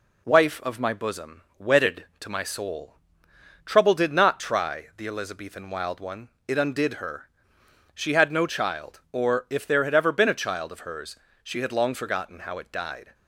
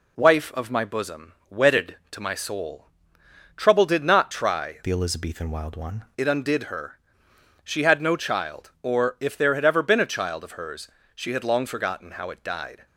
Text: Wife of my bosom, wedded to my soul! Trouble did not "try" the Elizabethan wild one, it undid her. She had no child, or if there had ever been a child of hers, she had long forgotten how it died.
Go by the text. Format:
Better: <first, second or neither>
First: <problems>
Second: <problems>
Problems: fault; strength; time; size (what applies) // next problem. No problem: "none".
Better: first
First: none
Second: changes voice from "the" to "one"; from 4.8 to 6.0 s; 1.2 s long